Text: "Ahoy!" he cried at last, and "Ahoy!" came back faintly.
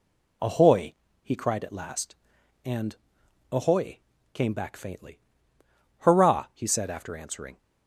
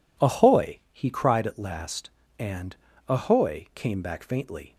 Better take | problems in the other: second | pauses between "and" and "Ahoy"; noticeable; at 2.9 s; 0.56 s long; slight in the second // goes on to say "Hurrah he said after answering"; from 5.9 s on; 1.5 s long

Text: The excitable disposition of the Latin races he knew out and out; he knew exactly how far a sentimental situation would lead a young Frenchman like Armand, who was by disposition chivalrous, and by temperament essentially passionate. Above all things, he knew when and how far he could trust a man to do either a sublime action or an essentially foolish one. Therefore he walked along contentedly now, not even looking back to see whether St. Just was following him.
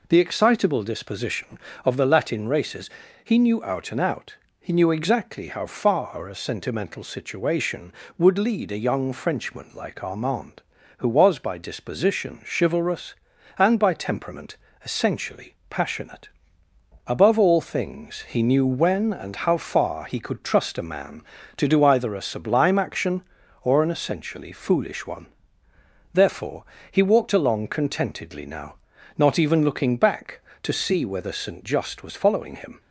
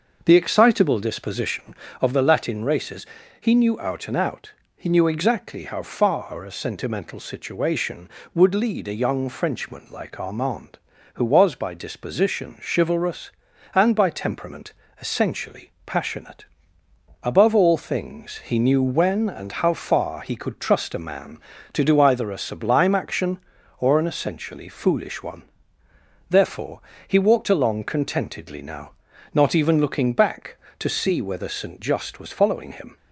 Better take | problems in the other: first | starts louder than the rest; until 1.7 s; 6 dB // pauses between "races" and "he"; slight; at 3.0 s; 0.34 s long; slight in the first // pauses between "temperament" and "essentially"; slight; at 14.7 s; 0.28 s long; slight in the first // pauses between "Therefore" and "he"; slight; at 26.7 s; 0.28 s long; slight in the first

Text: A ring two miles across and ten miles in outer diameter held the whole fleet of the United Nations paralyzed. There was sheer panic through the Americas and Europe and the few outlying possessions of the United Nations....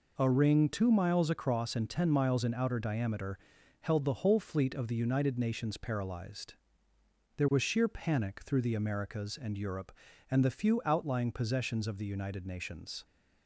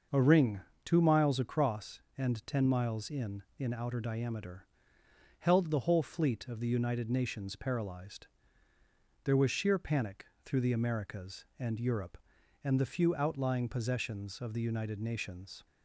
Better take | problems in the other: first | starts louder than the rest; noticeable; until 1.3 s; 6 dB // pauses between "ring" and "two"; slight; at 0.6 s; 0.24 s long // says "in" twice; at 3.5 s // pauses between "diameter" and "held"; noticeable; at 4.6 s; 0.74 s long; also in the first // pauses between "panic" and "through"; slight; at 10.2 s; 0.21 s long

